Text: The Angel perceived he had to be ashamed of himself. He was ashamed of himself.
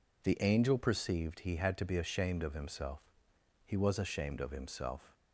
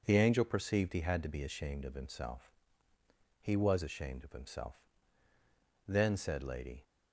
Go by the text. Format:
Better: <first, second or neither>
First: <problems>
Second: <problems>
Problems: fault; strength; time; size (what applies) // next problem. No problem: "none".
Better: first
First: none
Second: goes on to say "Then said Lady"; noticeable; from 5.8 s on; 0.96 s long